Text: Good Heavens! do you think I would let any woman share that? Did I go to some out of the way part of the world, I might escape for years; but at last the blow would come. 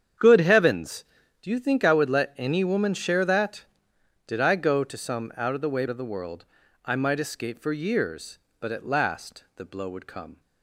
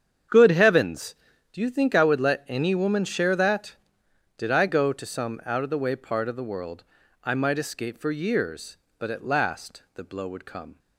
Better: second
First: starts louder than the rest; strong; until 1.6 s; 8.5 dB // skips "part"; at 5.8 s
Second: starts louder than the rest; strong; until 1.7 s; 8 dB

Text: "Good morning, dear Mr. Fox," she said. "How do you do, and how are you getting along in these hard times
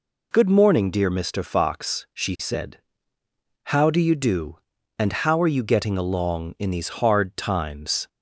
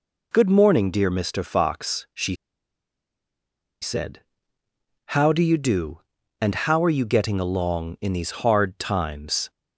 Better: first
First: none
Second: pauses between "she" and "said"; strong; at 2.3 s; 1.4 s long

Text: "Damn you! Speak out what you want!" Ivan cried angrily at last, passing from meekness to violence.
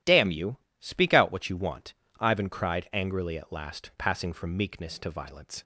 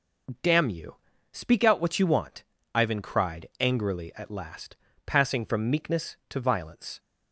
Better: neither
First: none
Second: none

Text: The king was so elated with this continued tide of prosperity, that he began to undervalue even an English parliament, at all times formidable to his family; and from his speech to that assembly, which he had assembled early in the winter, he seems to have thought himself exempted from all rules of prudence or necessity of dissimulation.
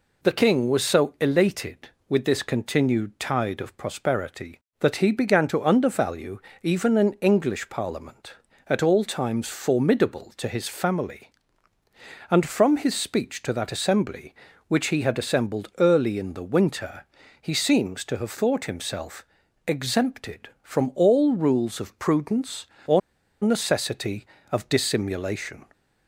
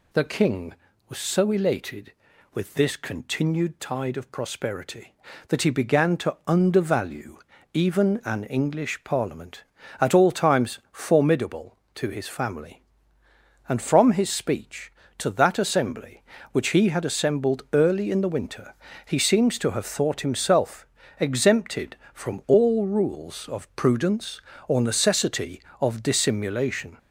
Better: second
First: pauses between "undervalue" and "even"; slight; at 6.3 s; 0.24 s long // pauses between "himself" and "exempted"; at 19.2 s; 0.42 s long // pauses between "or" and "necessity"; at 23.0 s; 0.43 s long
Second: pauses between "undervalue" and "even"; slight; at 7.3 s; 0.34 s long // pauses between "himself" and "exempted"; slight; at 20.8 s; 0.32 s long

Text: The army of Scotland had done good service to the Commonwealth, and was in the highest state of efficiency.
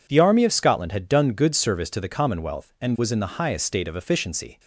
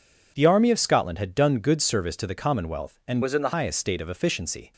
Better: first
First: none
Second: changes voice from "was" to "the"; from 3.2 to 3.5 s; 0.3 s long

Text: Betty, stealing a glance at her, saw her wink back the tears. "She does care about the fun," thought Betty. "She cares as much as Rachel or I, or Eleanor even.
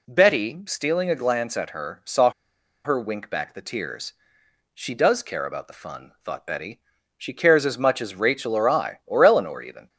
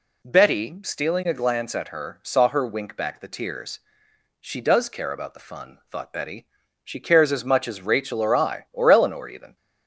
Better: second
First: pauses between "saw" and "her"; noticeable; at 2.2 s; 0.55 s long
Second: none

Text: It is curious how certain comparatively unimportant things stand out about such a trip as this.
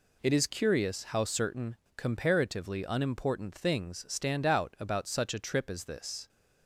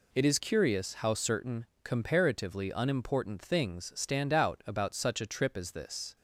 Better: neither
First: pauses between "certain" and "comparatively"; slight; at 1.7 s; 0.20 s long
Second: pauses between "certain" and "comparatively"; slight; at 1.6 s; 0.18 s long

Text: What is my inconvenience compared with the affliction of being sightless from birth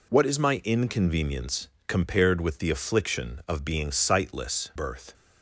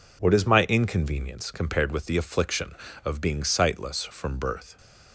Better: second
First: pauses between "inconvenience" and "compared"; slight; at 1.6 s; 0.18 s long // skips "from"; at 4.7 s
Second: none

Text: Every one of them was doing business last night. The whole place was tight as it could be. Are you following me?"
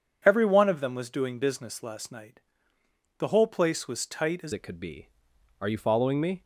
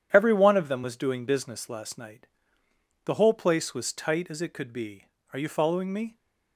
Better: second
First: changes voice at "it"; from 4.5 s on; 1.9 s long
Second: none

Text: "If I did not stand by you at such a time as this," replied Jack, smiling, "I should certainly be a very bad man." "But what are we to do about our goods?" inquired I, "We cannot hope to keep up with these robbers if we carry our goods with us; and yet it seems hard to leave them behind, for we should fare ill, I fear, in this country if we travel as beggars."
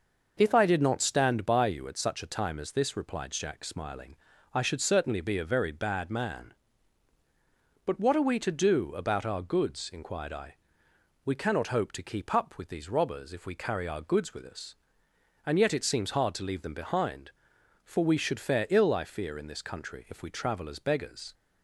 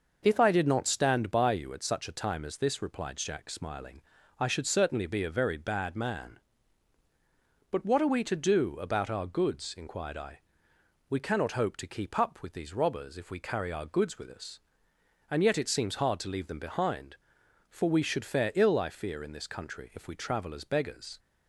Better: neither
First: none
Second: none

